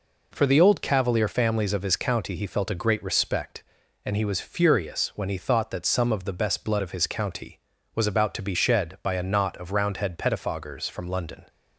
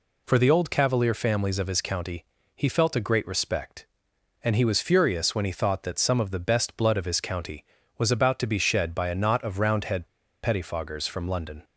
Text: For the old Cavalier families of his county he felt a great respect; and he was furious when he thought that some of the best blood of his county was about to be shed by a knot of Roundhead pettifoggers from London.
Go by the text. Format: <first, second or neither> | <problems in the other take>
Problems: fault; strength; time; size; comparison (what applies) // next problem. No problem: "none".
first | pauses between "county" and "he"; slight; at 2.2 s; 0.32 s long // pauses between "Roundhead" and "pettifoggers"; at 10.0 s; 0.36 s long